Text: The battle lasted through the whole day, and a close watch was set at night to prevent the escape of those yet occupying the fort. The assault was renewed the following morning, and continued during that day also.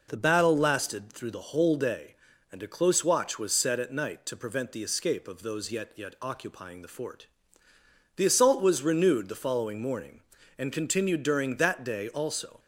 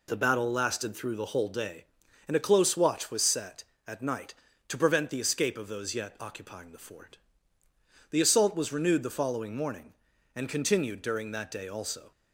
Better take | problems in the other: second | says "yet" twice; at 5.9 s

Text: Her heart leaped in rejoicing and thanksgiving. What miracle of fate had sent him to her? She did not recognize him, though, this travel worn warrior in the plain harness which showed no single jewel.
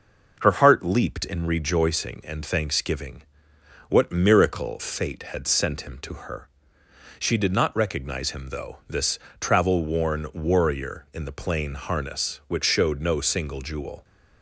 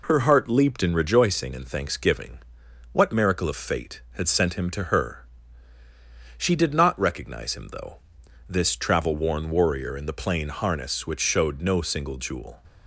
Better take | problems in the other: second | skips "of"; at 4.8 s // pauses between "this" and "travel"; slight; at 9.1 s; 0.22 s long

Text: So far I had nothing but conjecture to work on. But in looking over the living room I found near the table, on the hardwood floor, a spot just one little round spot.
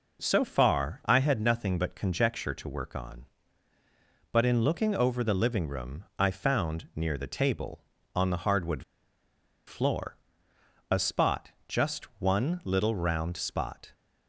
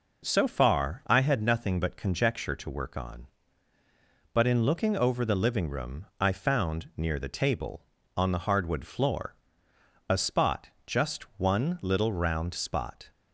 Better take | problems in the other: second | pauses between "hardwood" and "floor"; noticeable; at 8.8 s; 0.84 s long // pauses between "spot" and "just"; slight; at 11.4 s; 0.18 s long; slight in the second

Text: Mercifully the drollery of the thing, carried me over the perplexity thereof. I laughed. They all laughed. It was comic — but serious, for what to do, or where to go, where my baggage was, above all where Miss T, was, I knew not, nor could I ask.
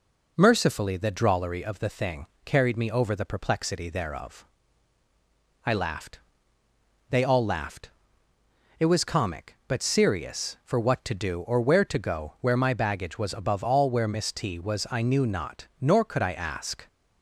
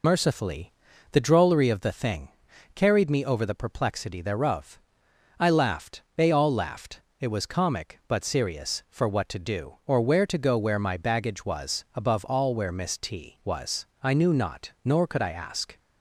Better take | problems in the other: first | loses the start of "Mercifully"; at 0.0 s; 45 ms // pauses between "Mercifully" and "the"; at 0.7 s; 0.40 s long

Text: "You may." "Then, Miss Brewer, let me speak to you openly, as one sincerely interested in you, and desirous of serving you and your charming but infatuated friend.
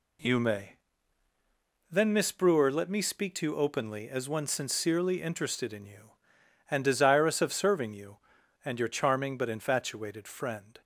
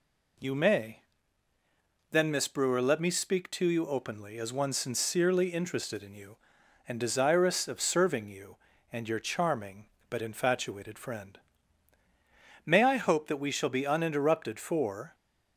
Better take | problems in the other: first | goes on to say "May I hope that we shall be uninterrupted for"; strong; from 12.6 s on; 2.5 s long

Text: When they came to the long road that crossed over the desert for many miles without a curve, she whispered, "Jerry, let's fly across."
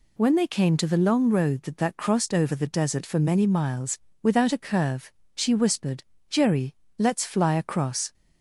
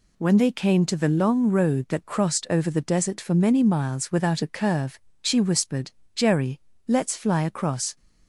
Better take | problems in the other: second | says "that" twice; at 1.7 s // pauses between "miles" and "without"; slight; at 3.9 s; 0.24 s long

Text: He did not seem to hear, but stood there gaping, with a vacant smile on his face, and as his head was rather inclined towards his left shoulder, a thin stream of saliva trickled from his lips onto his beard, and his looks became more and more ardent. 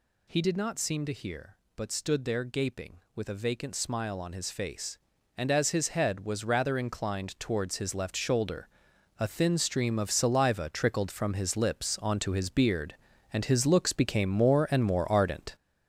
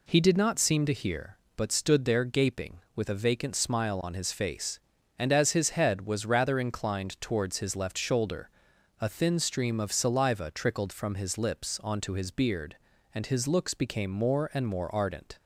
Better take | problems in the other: second | gets louder; strong; throughout; 7.5 dB

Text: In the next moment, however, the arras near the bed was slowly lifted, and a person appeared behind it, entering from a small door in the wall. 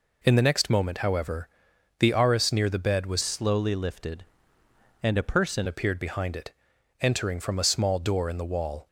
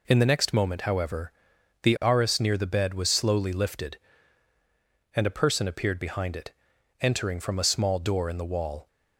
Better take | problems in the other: second | changes voice from "slowly" to "person"; from 3.2 to 5.6 s; 2.4 s long

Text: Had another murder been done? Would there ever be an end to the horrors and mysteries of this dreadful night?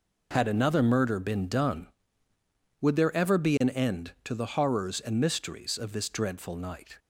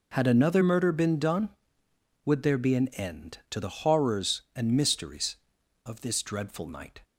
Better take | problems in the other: first | skips "ever"; at 2.5 s

